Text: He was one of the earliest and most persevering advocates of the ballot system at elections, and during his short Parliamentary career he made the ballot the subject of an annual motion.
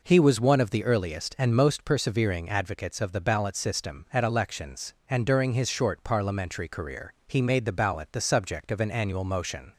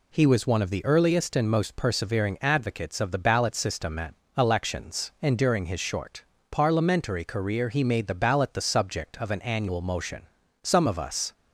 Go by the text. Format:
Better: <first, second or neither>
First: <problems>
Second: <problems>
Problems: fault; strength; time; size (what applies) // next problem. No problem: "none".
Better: first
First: none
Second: pauses between "at" and "elections"; slight; at 4.1 s; 0.24 s long // pauses between "short" and "Parliamentary"; slight; at 6.2 s; 0.26 s long // goes on to say "Some of us"; noticeable; from 10.6 s on; 0.68 s long